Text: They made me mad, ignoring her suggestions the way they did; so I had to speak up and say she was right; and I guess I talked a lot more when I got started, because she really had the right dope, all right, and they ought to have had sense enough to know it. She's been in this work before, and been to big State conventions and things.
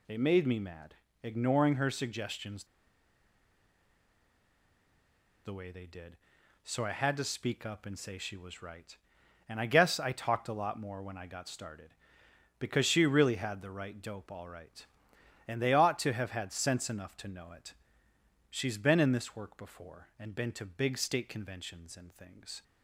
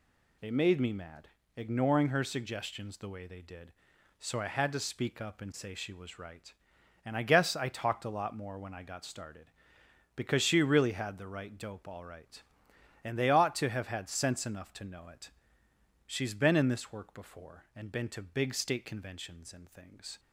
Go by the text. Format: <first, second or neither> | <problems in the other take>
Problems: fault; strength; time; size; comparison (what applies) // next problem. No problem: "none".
second | pauses between "suggestions" and "the"; strong; at 2.6 s; 2.8 s long